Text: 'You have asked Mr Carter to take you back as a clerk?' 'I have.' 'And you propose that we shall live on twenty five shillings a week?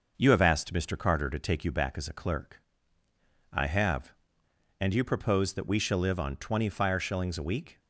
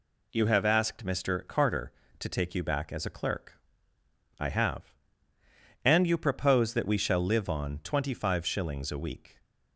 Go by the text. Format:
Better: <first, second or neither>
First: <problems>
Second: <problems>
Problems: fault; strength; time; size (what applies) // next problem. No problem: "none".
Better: second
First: starts louder than the rest; noticeable; until 1.1 s; 6 dB // says "fire" for "five"; at 6.6 s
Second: none